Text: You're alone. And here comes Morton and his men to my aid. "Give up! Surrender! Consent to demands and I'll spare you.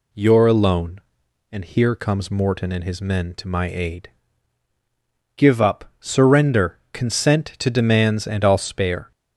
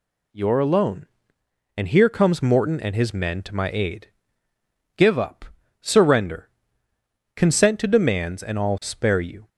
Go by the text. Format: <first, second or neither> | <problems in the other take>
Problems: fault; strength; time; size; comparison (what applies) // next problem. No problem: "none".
second | stops before "you"; at 9.1 s